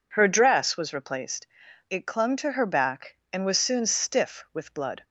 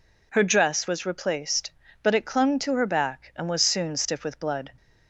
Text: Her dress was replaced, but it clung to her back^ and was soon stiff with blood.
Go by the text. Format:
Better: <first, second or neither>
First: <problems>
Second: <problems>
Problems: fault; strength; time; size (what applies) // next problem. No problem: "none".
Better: second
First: skips "but"; at 1.6 s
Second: none